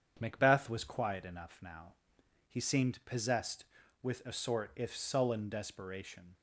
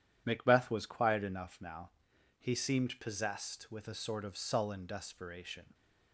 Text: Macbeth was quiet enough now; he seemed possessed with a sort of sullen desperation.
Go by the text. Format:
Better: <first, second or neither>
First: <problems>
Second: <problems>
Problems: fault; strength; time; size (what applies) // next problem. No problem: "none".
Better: second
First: starts louder than the rest; strong; until 1.2 s; 8 dB // says "if" for "of"; at 4.7 s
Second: none